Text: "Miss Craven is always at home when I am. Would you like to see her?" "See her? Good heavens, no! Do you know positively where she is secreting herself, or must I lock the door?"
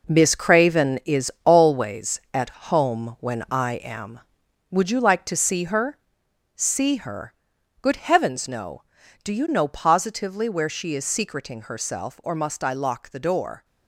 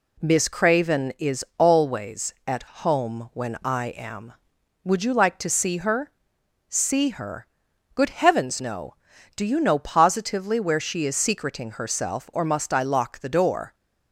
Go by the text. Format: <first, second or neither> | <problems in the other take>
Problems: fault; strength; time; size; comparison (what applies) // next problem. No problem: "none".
second | gets quieter; strong; throughout; 9 dB // pauses between "at" and "home"; slight; at 2.4 s; 0.20 s long; slight in the second